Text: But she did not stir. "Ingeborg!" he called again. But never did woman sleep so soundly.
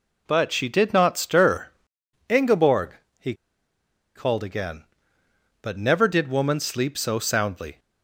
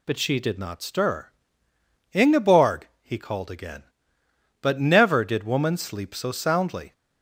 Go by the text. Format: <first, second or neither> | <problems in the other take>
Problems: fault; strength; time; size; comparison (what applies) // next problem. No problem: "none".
second | pauses between "he" and "called"; noticeable; at 3.3 s; 0.81 s long